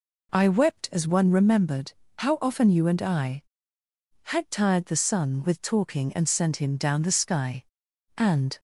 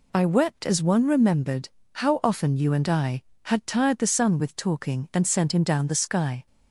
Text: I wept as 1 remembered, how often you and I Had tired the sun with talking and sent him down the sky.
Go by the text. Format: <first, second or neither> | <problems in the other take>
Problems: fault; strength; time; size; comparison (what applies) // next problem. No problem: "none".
second | goes on to say "And"; slight; from 8.1 s on; 0.44 s long